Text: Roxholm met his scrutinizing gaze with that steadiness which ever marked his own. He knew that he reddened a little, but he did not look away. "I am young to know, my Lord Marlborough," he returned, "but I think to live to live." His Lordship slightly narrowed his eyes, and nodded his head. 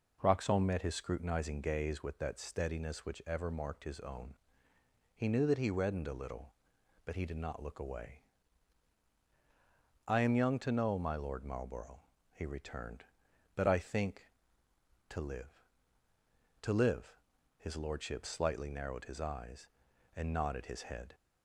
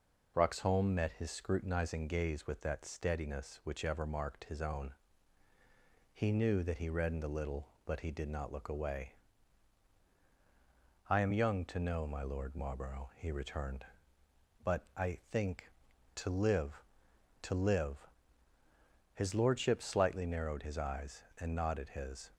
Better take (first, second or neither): first